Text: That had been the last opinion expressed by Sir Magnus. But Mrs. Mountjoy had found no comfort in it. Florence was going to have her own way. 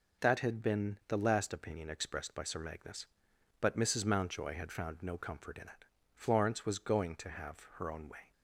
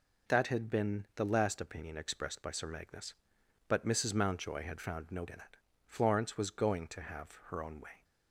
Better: first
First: none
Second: skips "comfort"; at 5.2 s

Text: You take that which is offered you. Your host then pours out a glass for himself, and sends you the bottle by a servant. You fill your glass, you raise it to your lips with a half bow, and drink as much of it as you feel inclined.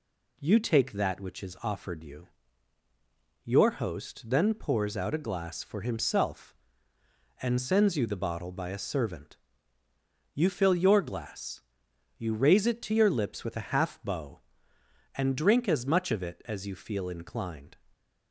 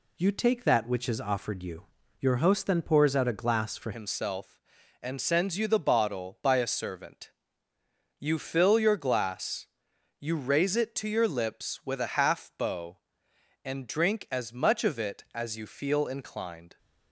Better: first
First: none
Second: changes voice at "himself"; from 3.9 s on; 12.8 s long

